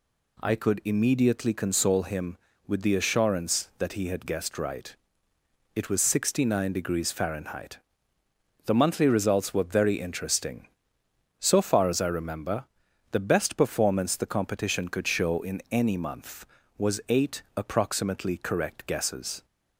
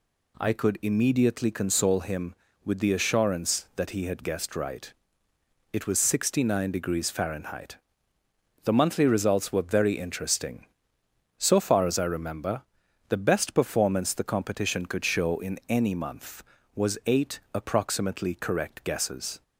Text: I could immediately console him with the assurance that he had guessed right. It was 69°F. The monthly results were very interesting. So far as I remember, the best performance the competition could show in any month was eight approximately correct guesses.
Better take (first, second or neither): neither